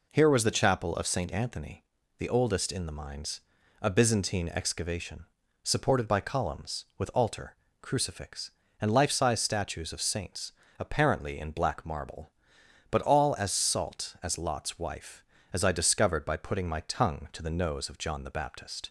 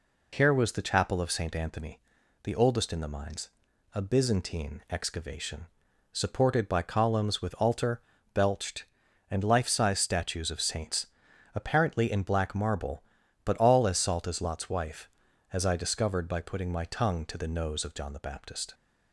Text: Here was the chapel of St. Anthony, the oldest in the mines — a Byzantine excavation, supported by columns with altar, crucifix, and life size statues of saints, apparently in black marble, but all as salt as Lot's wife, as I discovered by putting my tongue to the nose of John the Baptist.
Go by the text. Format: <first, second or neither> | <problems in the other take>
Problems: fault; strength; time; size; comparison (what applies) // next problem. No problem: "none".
first | says "belched" for "crucifix"; at 8.3 s